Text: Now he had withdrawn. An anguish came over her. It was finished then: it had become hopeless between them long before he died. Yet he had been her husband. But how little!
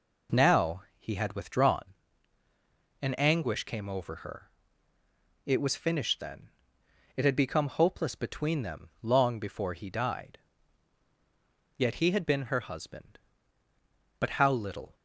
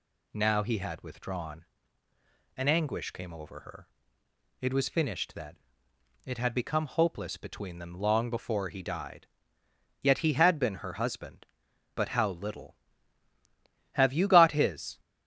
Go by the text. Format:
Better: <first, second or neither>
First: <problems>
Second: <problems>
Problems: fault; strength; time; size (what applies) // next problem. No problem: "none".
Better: first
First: none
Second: goes on to say "Have you got his"; noticeable; from 13.9 s on; 1.0 s long